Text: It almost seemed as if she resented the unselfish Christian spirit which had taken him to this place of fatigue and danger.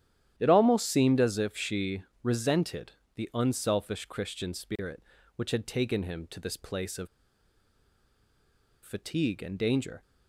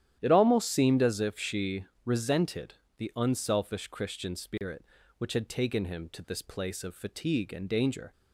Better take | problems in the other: second | starts louder than the rest; strong; until 1.3 s; 11 dB; strong in the second // pauses between "she" and "resented"; slight; at 2.0 s; 0.20 s long; slight in the second // pauses between "resented" and "the"; slight; at 2.9 s; 0.22 s long; slight in the second // pauses between "of" and "fatigue"; strong; at 7.0 s; 1.7 s long

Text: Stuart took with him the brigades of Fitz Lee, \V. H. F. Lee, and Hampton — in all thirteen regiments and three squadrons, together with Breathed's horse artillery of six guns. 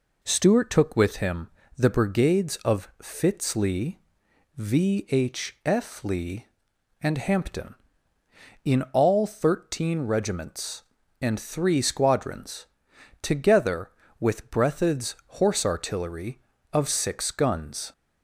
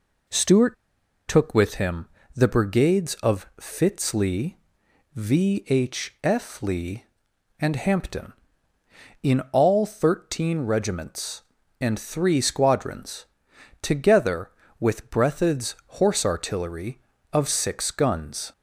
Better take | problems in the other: first | pauses between "Stuart" and "took"; noticeable; at 0.7 s; 0.52 s long // pauses between "him" and "the"; slight; at 2.0 s; 0.28 s long; slight in the first

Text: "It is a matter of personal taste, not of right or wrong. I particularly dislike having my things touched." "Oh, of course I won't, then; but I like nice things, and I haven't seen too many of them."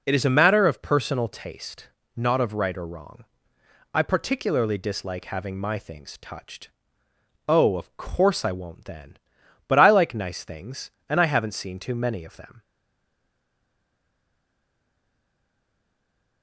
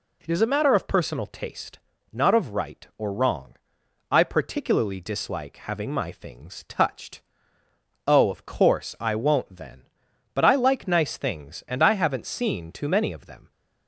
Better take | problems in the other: second | stays silent after the last word; strong; from 12.6 s on; 3.8 s long

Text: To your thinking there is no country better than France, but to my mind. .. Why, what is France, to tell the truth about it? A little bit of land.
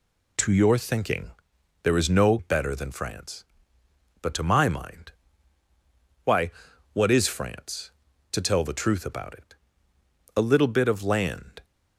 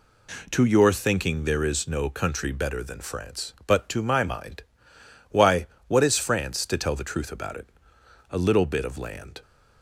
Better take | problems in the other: second | pauses between "thinking" and "there"; noticeable; at 1.2 s; 0.54 s long // skips "country"; at 2.3 s

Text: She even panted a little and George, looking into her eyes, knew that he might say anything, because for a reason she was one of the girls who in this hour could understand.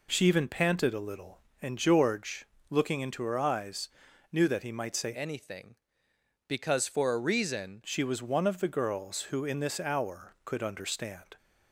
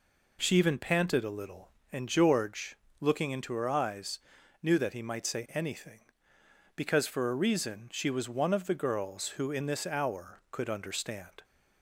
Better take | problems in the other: second | changes voice from "anything" to "reason"; from 5.1 to 7.8 s; 2.7 s long

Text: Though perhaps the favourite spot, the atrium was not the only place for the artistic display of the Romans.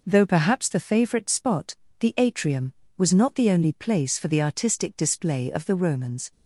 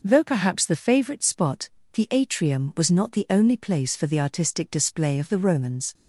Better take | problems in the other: neither | none

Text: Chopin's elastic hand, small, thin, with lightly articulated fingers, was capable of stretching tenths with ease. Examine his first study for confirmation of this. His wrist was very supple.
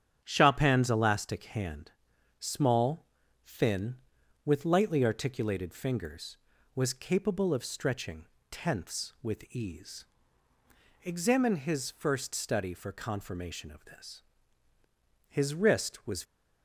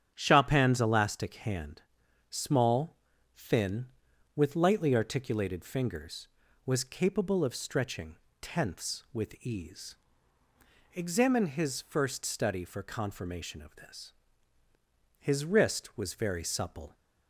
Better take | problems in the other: second | starts louder than the rest; strong; until 1.2 s; 8.5 dB; strong in the second // pauses between "stretching" and "tenths"; slight; at 8.2 s; 0.24 s long; slight in the second // stops before "very supple"; at 16.2 s

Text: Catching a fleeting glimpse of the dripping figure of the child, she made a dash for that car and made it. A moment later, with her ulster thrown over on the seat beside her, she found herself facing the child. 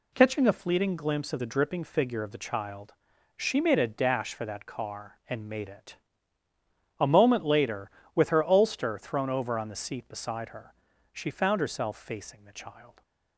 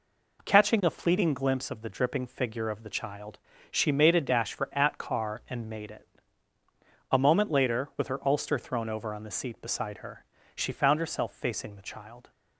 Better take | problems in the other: first | says "at" for "that"; at 4.7 s

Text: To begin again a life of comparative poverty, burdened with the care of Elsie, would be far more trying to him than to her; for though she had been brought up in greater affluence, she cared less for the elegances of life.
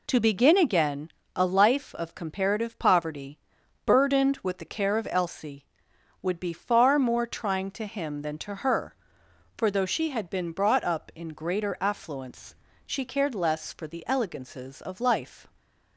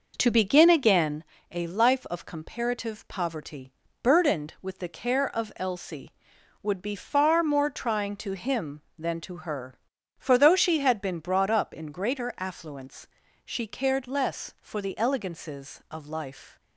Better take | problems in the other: first | starts louder than the rest; noticeable; until 1.3 s; 5.5 dB // pauses between "again" and "a"; slight; at 1.2 s; 0.28 s long; slight in the first

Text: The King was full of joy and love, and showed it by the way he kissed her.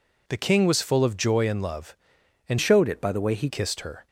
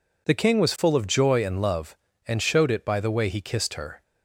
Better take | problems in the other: second | changes voice from "showed" to "he"; from 2.6 to 3.4 s; 0.8 s long

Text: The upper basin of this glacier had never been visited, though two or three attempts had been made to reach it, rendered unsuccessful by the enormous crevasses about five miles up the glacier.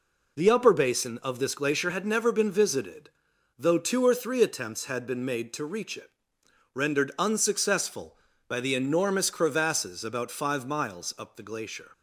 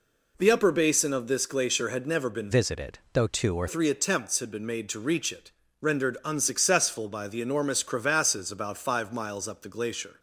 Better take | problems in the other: first | changes voice from "visited" to "or"; from 2.5 to 3.6 s; 1.1 s long

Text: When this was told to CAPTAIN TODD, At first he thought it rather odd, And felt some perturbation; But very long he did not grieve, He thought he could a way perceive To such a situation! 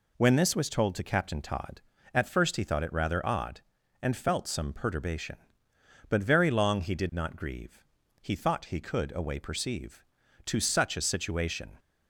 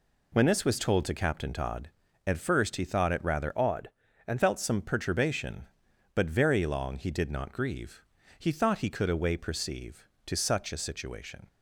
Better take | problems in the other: first | changes voice from "odd" to "And"; from 3.5 to 4.4 s; 0.9 s long

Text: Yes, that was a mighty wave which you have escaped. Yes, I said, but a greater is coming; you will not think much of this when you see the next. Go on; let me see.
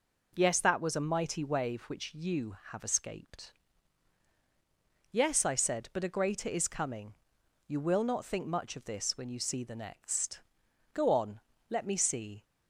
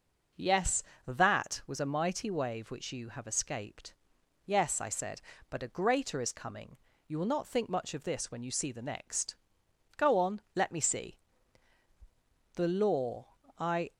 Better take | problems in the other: first | goes on to say "The law I"; from 12.5 s on; 1.3 s long

